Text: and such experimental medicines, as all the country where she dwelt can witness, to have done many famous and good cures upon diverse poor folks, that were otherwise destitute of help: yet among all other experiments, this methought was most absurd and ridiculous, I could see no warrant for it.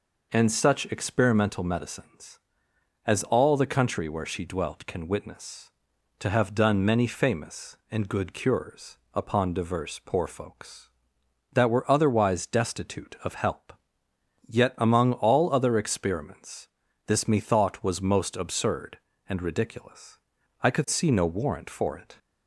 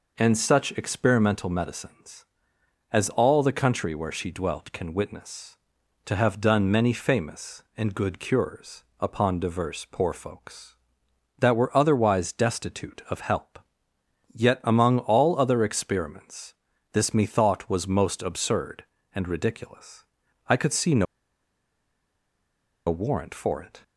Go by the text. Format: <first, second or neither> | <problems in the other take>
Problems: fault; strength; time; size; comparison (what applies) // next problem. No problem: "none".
first | pauses between "cures" and "upon"; slight; at 8.8 s; 0.16 s long; slight in the first // pauses between "no" and "warrant"; strong; at 21.0 s; 1.8 s long